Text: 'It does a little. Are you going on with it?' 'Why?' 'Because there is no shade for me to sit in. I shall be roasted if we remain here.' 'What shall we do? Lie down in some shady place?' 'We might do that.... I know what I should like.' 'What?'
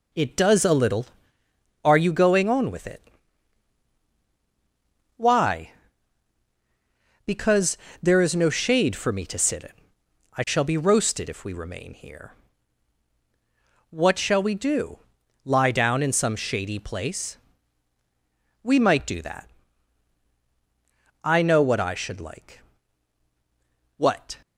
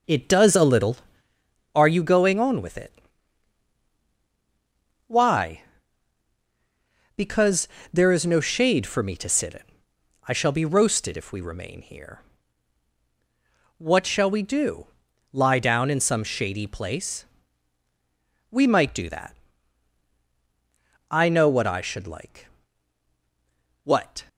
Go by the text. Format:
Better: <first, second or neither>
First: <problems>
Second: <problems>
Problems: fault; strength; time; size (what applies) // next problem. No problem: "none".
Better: first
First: pauses between "Because" and "there"; slight; at 7.7 s; 0.26 s long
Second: starts louder than the rest; noticeable; until 1.5 s; 5.5 dB // pauses between "Because" and "there"; slight; at 7.6 s; 0.26 s long